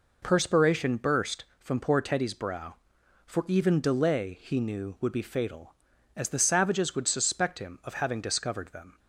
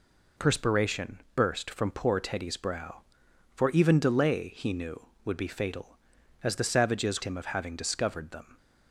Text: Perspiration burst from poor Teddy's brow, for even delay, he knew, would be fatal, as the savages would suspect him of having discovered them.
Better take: first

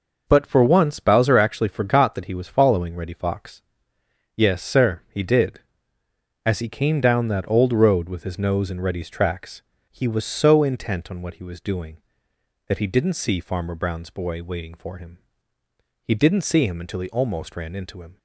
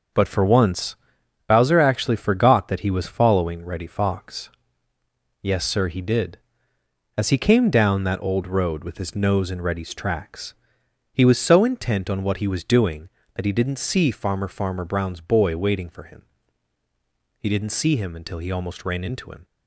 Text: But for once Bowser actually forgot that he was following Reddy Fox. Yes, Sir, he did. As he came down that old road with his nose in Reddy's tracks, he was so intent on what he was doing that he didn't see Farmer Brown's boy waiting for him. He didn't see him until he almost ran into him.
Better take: first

